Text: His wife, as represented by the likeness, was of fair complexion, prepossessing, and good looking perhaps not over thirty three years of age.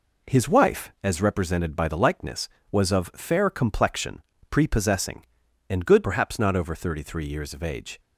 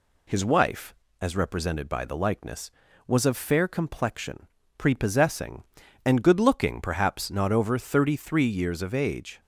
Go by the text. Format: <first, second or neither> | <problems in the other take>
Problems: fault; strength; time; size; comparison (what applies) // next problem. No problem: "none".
second | skips "looking"; at 6.0 s